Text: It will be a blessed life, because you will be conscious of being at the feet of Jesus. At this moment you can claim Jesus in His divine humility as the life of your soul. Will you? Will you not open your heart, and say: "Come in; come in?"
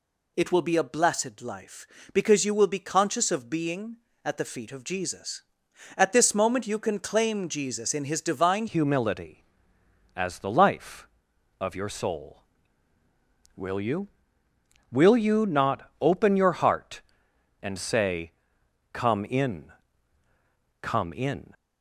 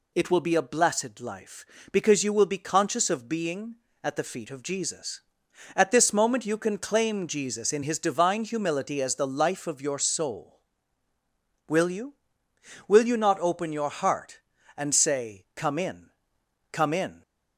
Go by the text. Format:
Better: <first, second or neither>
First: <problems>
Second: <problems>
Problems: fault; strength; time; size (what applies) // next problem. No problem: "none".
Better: second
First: changes voice at "humility"; from 8.6 s on; 12.9 s long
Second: none